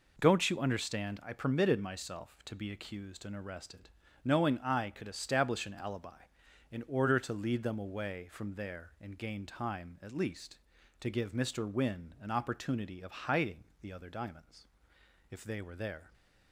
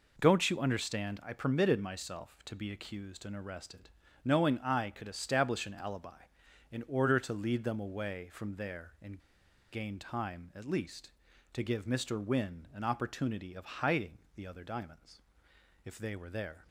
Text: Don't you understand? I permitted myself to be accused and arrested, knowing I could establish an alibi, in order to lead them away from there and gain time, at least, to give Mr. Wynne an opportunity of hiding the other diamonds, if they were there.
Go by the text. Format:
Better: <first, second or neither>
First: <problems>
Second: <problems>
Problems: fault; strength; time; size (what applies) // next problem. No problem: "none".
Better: first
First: pauses between "hiding" and "the"; slight; at 13.6 s; 0.16 s long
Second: pauses between "and" and "gain"; noticeable; at 9.1 s; 0.53 s long // pauses between "hiding" and "the"; slight; at 14.1 s; 0.16 s long